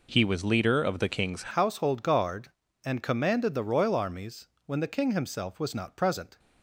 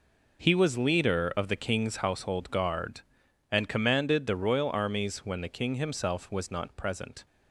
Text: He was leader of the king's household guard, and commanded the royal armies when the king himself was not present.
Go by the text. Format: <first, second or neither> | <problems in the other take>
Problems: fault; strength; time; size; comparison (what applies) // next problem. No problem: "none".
second | changes voice at "household"; from 1.5 s on; 4.8 s long // pauses between "armies" and "when"; slight; at 4.4 s; 0.18 s long